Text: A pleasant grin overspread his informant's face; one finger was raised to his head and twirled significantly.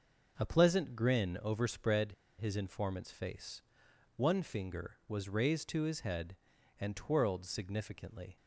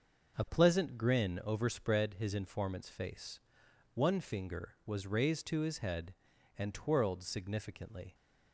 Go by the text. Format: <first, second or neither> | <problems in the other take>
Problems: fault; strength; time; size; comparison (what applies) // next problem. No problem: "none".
second | pauses between "overspread" and "his"; slight; at 2.1 s; 0.26 s long